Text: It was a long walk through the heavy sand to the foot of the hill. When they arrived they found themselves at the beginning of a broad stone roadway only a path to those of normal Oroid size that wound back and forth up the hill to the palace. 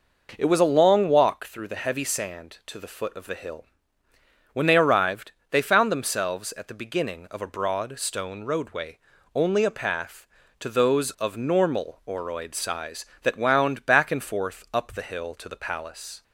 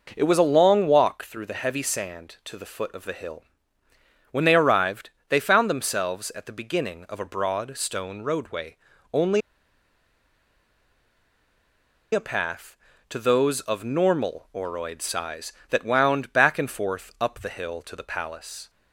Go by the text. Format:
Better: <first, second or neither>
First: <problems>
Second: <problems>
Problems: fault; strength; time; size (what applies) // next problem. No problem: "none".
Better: first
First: pauses between "arrived" and "they"; slight; at 5.3 s; 0.18 s long // pauses between "roadway" and "only"; slight; at 8.9 s; 0.36 s long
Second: pauses between "arrived" and "they"; slight; at 5.1 s; 0.18 s long // pauses between "roadway" and "only"; slight; at 8.7 s; 0.36 s long // pauses between "only" and "a"; strong; at 9.4 s; 2.7 s long